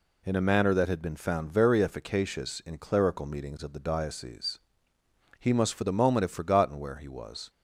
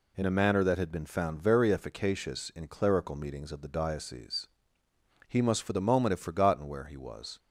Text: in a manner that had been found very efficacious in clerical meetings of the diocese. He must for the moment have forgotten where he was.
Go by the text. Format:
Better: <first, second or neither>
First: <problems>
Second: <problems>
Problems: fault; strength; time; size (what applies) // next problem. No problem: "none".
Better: neither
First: none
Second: none